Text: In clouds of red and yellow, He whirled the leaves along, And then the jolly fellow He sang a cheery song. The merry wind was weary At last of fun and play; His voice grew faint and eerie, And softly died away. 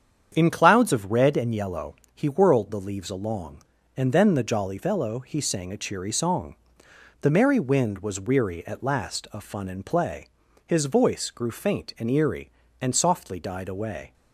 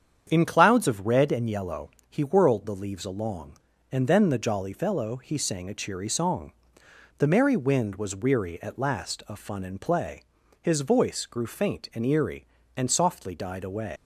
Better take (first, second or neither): first